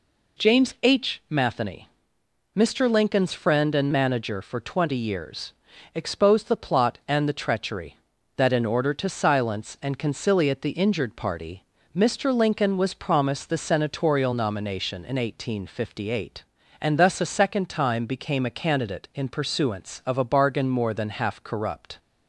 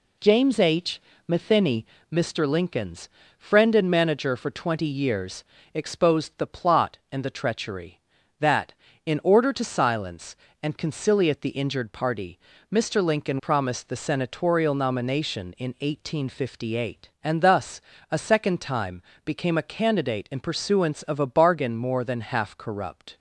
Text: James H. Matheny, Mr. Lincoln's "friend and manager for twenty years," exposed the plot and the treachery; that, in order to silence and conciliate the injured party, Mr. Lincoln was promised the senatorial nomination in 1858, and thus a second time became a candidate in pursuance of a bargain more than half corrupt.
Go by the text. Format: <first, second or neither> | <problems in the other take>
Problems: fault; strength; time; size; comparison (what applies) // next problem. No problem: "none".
first | pauses between "Lincoln's" and "friend"; slight; at 3.0 s; 0.30 s long // skips "was"; at 13.3 s // pauses between "thus" and "a"; slight; at 17.7 s; 0.32 s long // pauses between "time" and "became"; slight; at 19.0 s; 0.22 s long